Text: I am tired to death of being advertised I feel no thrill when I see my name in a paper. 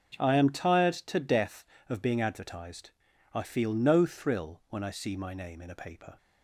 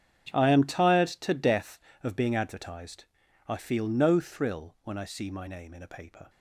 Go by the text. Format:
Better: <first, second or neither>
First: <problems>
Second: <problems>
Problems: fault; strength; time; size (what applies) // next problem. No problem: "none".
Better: first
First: starts louder than the rest; until 1.1 s; 6.5 dB // pauses between "advertised" and "I"; at 2.9 s; 0.42 s long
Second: gets quieter; strong; throughout; 16.5 dB // starts louder than the rest; strong; until 1.3 s; 8.5 dB // pauses between "advertised" and "I"; at 3.0 s; 0.42 s long